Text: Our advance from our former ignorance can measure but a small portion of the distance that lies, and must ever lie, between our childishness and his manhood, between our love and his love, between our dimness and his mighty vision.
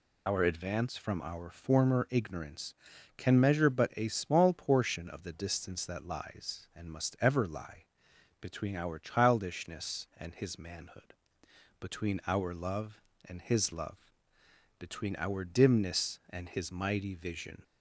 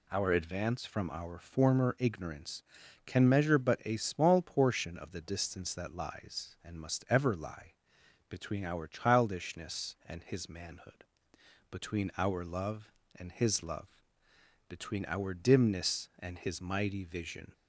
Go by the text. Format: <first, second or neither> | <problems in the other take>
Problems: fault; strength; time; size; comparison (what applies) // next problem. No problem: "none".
second | loses the start of "Our"; at 0.2 s; 55 ms